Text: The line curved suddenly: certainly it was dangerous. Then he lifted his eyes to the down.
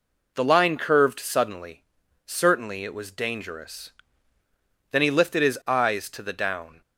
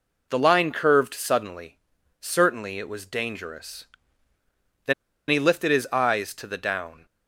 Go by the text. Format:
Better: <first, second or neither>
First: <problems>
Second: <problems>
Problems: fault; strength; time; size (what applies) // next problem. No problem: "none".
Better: first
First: none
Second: pauses between "Then" and "he"; slight; at 4.9 s; 0.35 s long